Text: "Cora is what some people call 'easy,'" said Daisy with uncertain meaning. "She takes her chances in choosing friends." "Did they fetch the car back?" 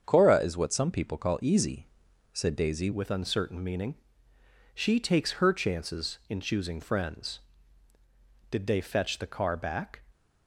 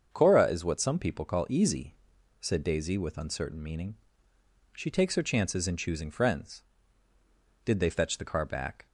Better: second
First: starts louder than the rest; strong; until 1.0 s; 7 dB // changes voice at "with"; from 2.9 s on; 7.1 s long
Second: starts louder than the rest; until 1.1 s; 7 dB

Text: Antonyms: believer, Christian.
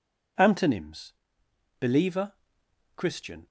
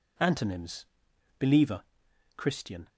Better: neither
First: none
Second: none

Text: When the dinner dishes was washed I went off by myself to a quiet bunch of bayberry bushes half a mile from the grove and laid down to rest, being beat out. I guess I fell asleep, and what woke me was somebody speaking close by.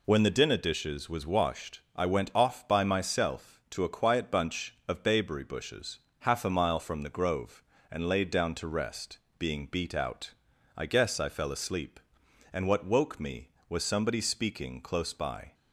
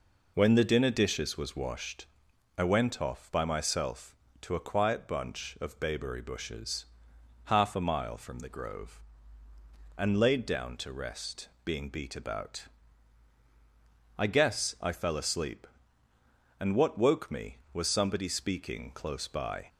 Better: first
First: pauses between "washed" and "I"; slight; at 1.7 s; 0.16 s long // pauses between "bushes" and "half"; slight; at 5.9 s; 0.22 s long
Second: pauses between "washed" and "I"; noticeable; at 2.0 s; 0.52 s long // pauses between "bushes" and "half"; noticeable; at 6.8 s; 0.58 s long // says "about" for "out"; at 12.1 s

